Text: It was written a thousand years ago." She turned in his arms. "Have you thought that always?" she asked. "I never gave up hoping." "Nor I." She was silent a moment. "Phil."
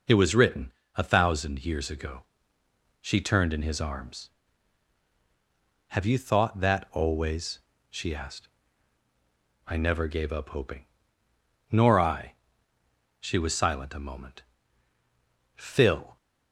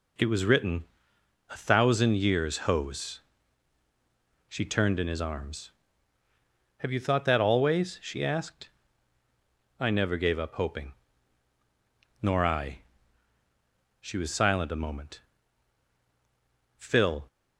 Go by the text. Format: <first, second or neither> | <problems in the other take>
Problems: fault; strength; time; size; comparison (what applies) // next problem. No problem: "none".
first | pauses between "written" and "a"; noticeable; at 0.8 s; 0.66 s long; slight in the first // says "hose" for "ago"; at 2.6 s